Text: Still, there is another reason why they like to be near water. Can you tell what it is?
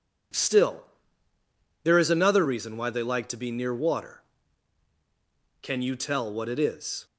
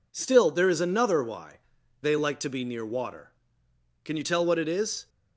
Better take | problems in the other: first | skips "reason"; at 1.2 s // pauses between "why" and "they"; at 1.5 s; 0.42 s long

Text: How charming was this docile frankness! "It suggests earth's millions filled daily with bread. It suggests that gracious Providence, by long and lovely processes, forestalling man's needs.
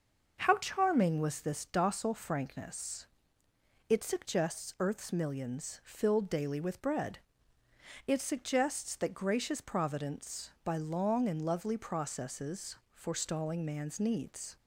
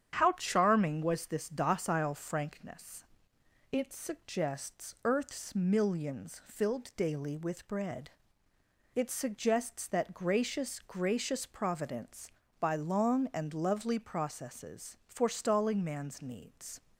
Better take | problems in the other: first | starts louder than the rest; strong; until 1.2 s; 9 dB // says "gracious" twice; at 10.8 s

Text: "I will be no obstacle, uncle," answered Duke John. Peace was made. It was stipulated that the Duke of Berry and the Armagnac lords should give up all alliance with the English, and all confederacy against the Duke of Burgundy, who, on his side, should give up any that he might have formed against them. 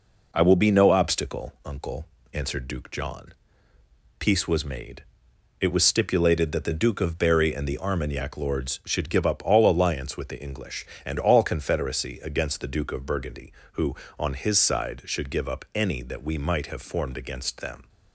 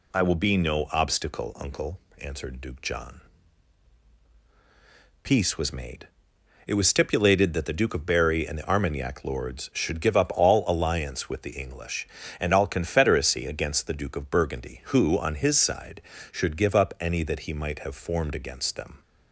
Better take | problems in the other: second | says "we" for "he"; at 16.2 s

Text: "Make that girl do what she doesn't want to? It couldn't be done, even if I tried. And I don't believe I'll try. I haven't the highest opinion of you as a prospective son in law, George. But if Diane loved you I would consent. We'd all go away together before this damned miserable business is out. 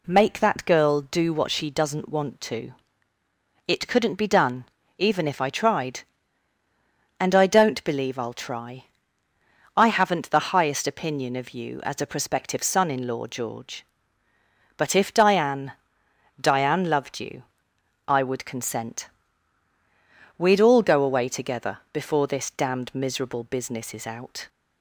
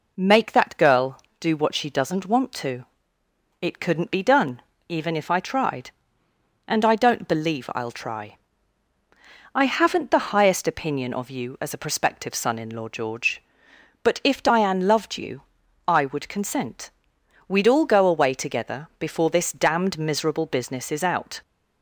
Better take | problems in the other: second | says "Diane" twice; at 16.4 s // pauses between "you" and "I"; noticeable; at 17.4 s; 0.62 s long; noticeable in the second

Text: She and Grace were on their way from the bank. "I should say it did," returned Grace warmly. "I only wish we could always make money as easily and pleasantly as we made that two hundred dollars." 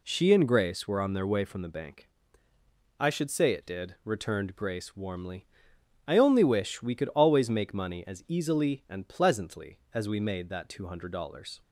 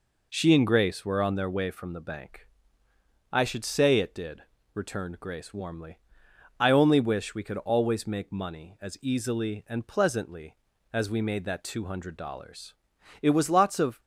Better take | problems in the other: first | goes on to say "It was lots of"; noticeable; from 13.2 s on; 0.78 s long

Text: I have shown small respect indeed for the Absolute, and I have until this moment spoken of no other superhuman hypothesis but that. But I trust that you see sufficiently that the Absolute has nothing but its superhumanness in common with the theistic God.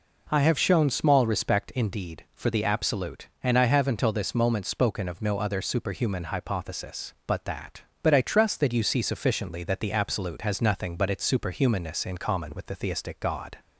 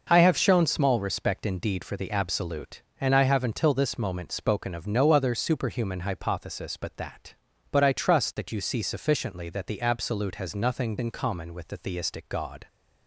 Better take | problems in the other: first | skips "but its superhumanness"; at 10.9 s

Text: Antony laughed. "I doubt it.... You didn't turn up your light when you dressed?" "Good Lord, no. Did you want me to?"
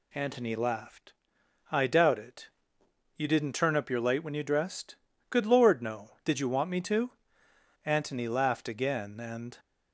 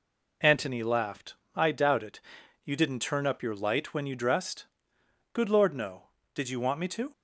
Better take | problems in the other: second | goes on to say "Antony laughed again and"; strong; from 7.8 s on; 1.7 s long

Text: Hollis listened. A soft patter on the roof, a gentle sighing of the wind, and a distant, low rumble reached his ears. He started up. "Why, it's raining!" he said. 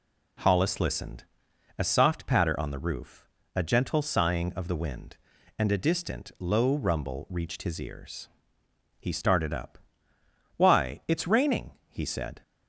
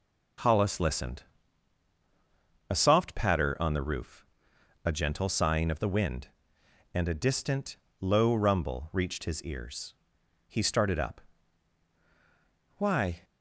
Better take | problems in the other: first | stops before "it's raining he said"; at 13.2 s

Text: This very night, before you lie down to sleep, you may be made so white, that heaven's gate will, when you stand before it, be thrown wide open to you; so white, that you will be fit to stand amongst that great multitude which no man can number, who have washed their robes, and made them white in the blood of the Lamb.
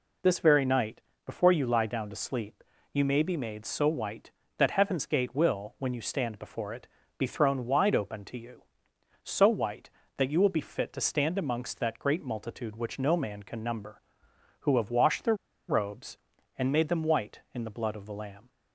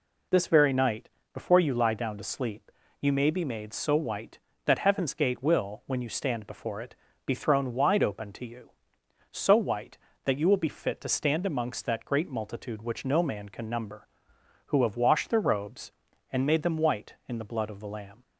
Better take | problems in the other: second | pauses between "their" and "robes"; slight; at 15.3 s; 0.33 s long

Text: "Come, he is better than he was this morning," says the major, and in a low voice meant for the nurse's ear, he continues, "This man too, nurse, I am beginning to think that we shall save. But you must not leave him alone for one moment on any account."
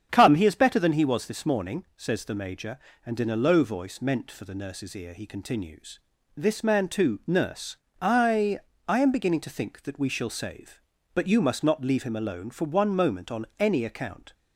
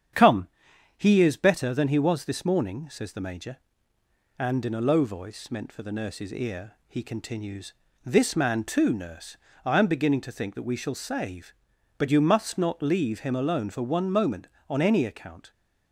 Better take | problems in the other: second | starts louder than the rest; strong; until 1.1 s; 8 dB; strong in the second // says "I" twice; at 8.8 s

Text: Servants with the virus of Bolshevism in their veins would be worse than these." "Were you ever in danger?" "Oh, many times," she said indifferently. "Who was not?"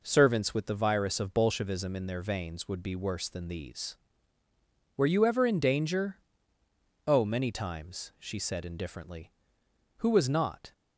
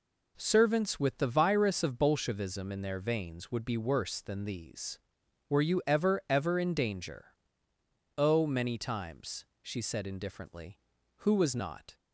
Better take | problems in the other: first | says "ever" twice; at 6.2 s

